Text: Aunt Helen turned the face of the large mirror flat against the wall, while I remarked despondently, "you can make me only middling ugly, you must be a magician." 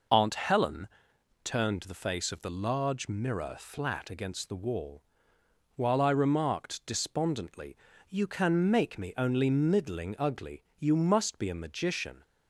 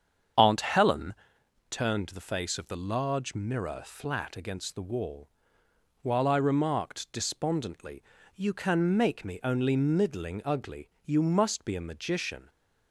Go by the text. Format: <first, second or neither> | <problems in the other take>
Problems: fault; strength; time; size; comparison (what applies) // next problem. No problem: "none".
first | starts louder than the rest; strong; until 1.3 s; 8 dB // pauses between "Helen" and "turned"; noticeable; at 1.1 s; 0.56 s long; noticeable in the first